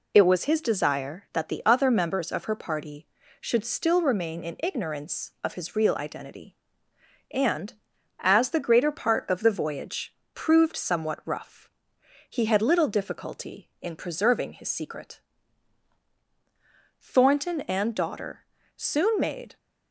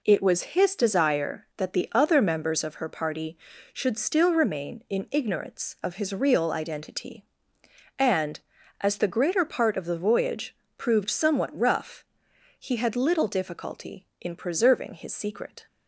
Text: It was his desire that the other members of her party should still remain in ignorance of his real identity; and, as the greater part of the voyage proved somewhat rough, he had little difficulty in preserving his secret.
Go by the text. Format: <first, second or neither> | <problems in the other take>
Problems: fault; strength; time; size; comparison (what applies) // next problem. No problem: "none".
second | pauses between "voyage" and "proved"; slight; at 10.1 s; 0.16 s long; slight in the second // goes on to say "Thornton and daughter soon made"; strong; from 17.0 s on; 2.5 s long